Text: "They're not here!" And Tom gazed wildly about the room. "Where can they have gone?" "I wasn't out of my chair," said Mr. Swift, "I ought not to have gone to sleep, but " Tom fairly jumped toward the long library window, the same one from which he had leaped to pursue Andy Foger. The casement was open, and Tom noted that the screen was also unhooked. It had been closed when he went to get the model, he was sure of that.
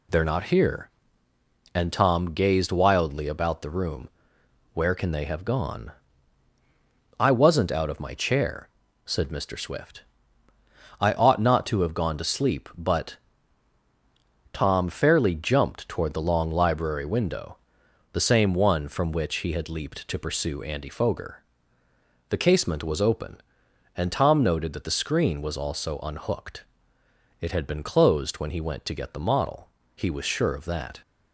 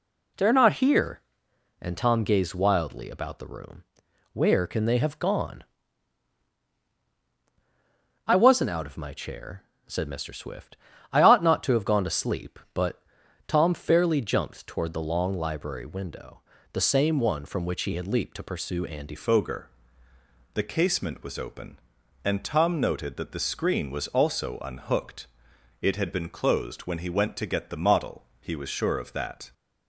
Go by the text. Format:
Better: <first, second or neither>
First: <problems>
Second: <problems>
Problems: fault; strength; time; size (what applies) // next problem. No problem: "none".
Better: first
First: none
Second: changes voice at "Foger"; from 19.1 s on; 10.4 s long